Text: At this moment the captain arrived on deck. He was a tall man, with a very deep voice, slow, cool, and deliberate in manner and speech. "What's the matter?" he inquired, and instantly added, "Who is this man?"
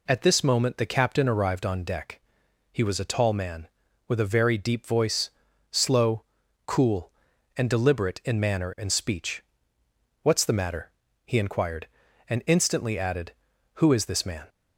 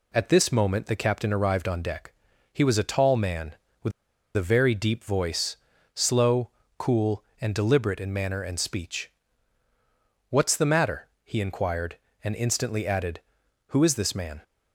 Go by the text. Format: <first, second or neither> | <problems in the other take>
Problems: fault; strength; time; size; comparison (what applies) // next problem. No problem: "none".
first | pauses between "with" and "a"; at 3.9 s; 0.45 s long